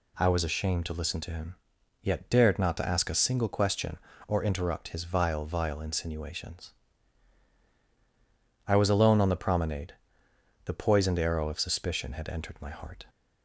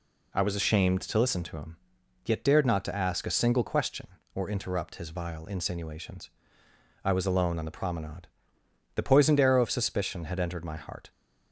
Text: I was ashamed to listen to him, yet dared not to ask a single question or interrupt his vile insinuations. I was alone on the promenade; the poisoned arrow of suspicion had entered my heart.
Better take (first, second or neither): second